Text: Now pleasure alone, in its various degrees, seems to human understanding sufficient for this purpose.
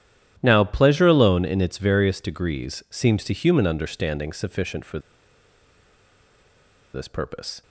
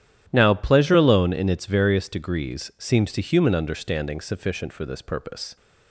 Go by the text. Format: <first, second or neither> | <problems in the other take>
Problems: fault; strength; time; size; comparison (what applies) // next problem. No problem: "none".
second | starts louder than the rest; strong; until 1.4 s; 11.5 dB; strong in the second // pauses between "for" and "this"; strong; at 4.9 s; 1.9 s long